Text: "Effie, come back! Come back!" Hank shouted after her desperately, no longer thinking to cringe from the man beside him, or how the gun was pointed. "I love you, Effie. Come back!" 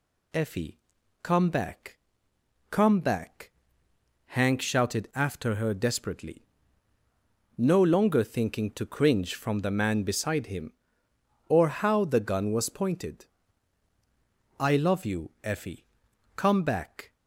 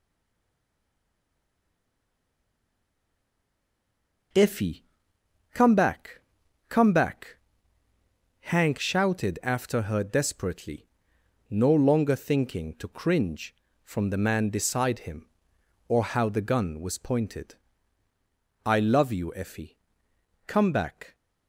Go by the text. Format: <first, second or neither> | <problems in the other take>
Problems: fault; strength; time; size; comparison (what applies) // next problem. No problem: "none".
first | stays silent before the first word; strong; until 4.3 s; 4.3 s long